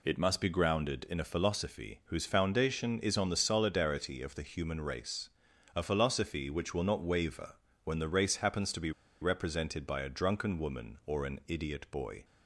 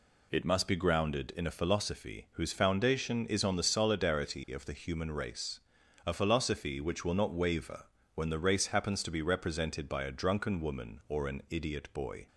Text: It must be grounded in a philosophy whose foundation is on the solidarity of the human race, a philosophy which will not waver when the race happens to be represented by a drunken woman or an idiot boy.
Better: second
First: pauses between "waver" and "when"; slight; at 7.5 s; 0.30 s long // pauses between "be" and "represented"; slight; at 8.9 s; 0.31 s long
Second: pauses between "waver" and "when"; slight; at 7.8 s; 0.30 s long

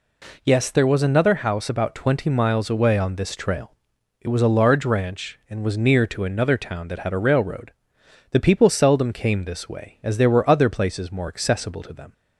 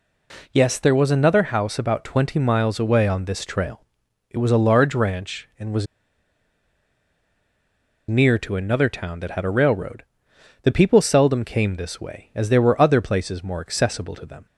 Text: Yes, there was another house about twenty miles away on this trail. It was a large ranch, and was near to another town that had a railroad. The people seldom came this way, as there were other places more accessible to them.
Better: first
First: none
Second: pauses between "was" and "near"; strong; at 5.8 s; 2.2 s long

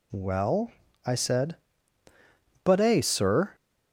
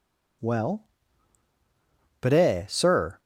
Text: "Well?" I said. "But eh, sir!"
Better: first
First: none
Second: skips "I said"; at 1.5 s

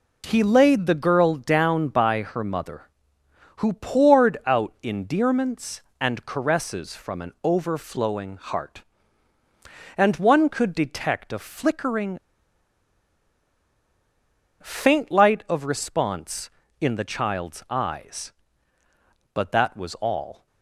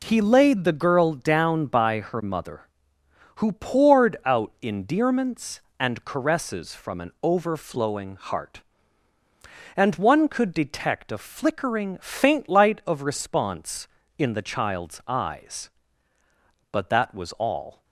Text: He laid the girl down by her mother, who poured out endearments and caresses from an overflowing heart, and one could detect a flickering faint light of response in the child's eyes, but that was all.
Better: second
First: pauses between "flickering" and "faint"; strong; at 12.1 s; 2.4 s long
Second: none

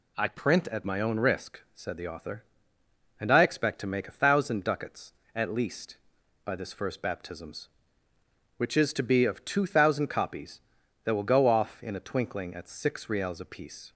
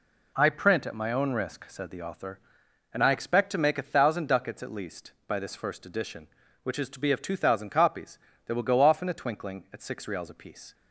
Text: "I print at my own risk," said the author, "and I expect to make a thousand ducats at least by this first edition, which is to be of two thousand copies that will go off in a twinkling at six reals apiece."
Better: second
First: says "baptisms" for "edition"; at 7.0 s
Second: none

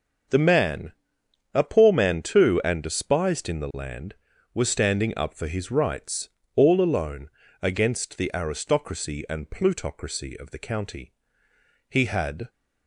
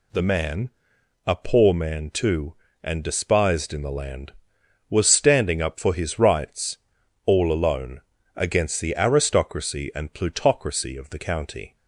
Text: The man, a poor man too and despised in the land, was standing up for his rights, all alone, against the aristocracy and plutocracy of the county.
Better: second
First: starts louder than the rest; until 1.9 s; 6.5 dB // goes on to say "He had"; from 11.8 s on; 0.60 s long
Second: none

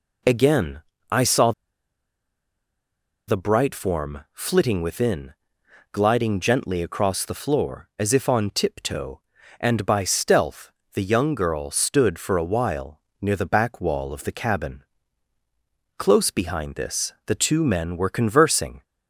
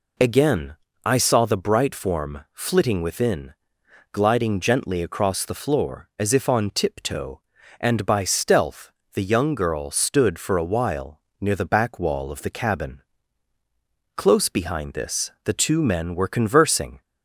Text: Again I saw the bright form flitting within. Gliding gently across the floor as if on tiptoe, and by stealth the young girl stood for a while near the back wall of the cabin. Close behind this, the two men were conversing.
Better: second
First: pauses between "Again" and "I"; slight; at 0.8 s; 0.30 s long // pauses between "saw" and "the"; strong; at 1.5 s; 1.7 s long // pauses between "stealth" and "the"; slight; at 10.7 s; 0.22 s long // pauses between "while" and "near"; slight; at 12.9 s; 0.20 s long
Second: pauses between "Again" and "I"; slight; at 0.7 s; 0.30 s long // pauses between "stealth" and "the"; slight; at 8.9 s; 0.22 s long // pauses between "while" and "near"; slight; at 11.1 s; 0.19 s long

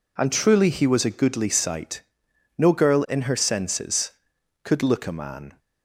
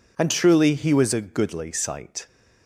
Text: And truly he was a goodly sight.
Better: second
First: goes on to say "No girl in her senses could look a man"; strong; from 2.5 s on; 3.0 s long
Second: none

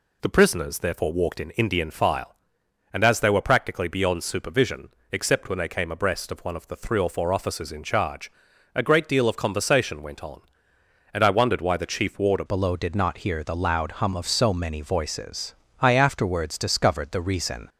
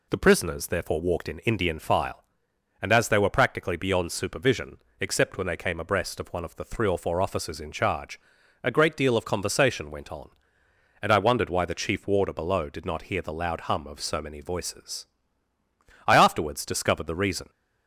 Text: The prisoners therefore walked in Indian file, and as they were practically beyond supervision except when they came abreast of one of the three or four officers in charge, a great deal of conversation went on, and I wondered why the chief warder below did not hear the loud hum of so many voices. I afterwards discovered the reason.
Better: second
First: pauses between "supervision" and "except"; slight; at 4.8 s; 0.22 s long // changes voice at "below"; from 12.4 s on; 5.2 s long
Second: pauses between "supervision" and "except"; slight; at 4.7 s; 0.22 s long

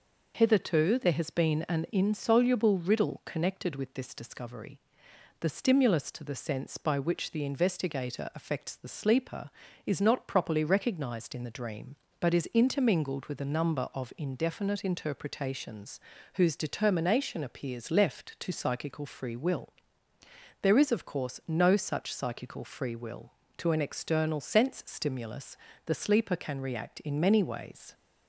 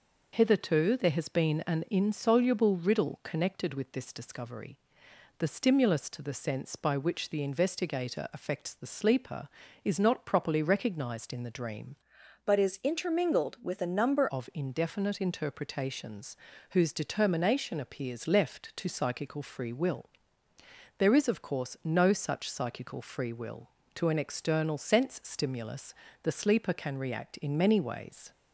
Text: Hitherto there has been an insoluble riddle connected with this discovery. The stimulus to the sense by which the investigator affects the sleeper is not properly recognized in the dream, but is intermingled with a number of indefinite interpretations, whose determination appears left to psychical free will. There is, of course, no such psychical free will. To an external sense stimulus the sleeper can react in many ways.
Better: first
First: pauses between "stimulus" and "the"; slight; at 25.5 s; 0.30 s long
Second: changes voice from "but" to "number"; from 12.4 to 14.2 s; 1.8 s long // pauses between "stimulus" and "the"; slight; at 25.9 s; 0.30 s long

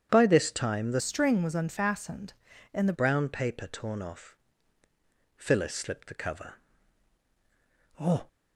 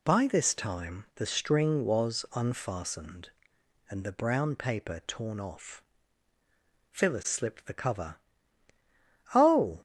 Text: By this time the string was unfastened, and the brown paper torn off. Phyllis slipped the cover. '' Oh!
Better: second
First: starts louder than the rest; strong; until 1.1 s; 10 dB // changes voice from "string" to "the"; from 0.9 to 2.9 s; 2.0 s long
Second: none

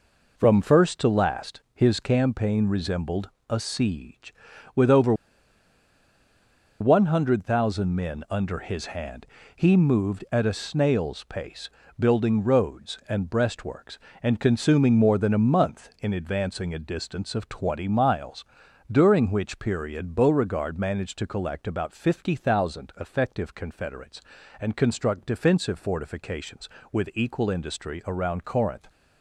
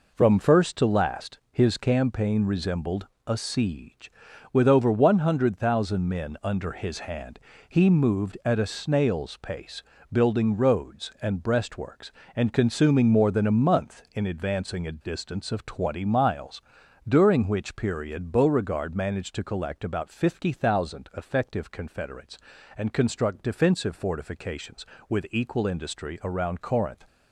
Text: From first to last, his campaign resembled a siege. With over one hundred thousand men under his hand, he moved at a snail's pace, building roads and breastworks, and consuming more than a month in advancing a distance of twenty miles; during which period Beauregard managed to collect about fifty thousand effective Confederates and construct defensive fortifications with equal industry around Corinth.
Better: second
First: pauses between "resembled" and "a"; slight; at 3.2 s; 0.18 s long // pauses between "over" and "one"; strong; at 5.1 s; 1.6 s long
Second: pauses between "resembled" and "a"; slight; at 3.0 s; 0.18 s long

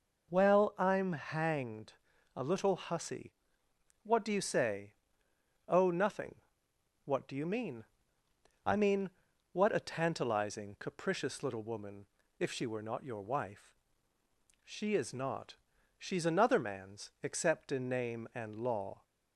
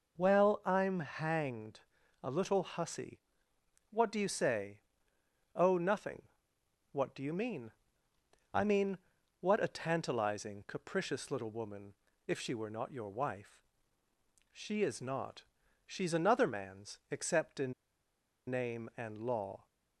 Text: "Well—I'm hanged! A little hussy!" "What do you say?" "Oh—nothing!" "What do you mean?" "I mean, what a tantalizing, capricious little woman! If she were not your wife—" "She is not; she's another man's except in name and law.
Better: first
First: none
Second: pauses between "in" and "name"; noticeable; at 17.7 s; 0.76 s long

